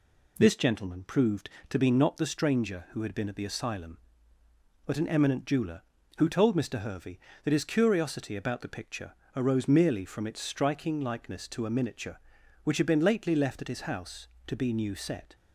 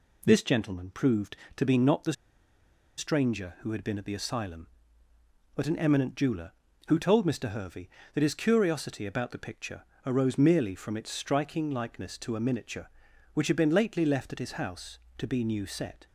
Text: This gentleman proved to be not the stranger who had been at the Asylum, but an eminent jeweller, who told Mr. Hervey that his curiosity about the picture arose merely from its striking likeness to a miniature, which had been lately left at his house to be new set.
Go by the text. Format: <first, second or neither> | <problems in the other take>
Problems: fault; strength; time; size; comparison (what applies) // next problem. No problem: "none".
first | pauses between "the" and "stranger"; noticeable; at 2.1 s; 0.84 s long // pauses between "picture" and "arose"; slight; at 9.8 s; 0.22 s long; slight in the first